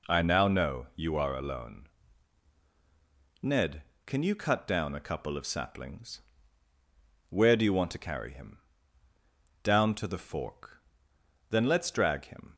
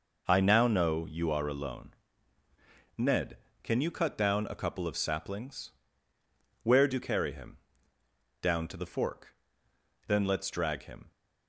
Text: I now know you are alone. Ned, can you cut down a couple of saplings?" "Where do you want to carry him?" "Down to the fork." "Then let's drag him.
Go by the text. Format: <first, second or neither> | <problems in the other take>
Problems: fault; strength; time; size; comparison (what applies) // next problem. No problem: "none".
first | skips "you want to"; at 6.9 s